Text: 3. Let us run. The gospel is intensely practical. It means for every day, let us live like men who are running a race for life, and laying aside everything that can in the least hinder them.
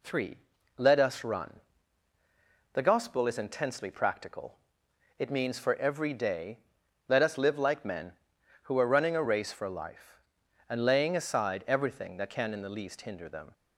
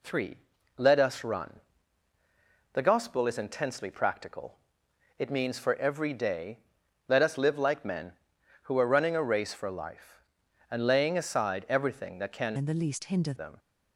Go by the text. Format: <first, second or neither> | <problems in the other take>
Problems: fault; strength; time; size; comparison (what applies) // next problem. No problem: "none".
first | changes voice from "in" to "hinder"; from 12.5 to 13.3 s; 0.8 s long